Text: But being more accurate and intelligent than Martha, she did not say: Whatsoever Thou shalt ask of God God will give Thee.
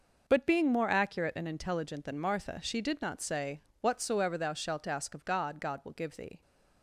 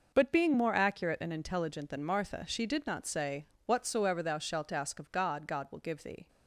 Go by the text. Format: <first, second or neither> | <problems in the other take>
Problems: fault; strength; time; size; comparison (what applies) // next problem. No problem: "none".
neither | none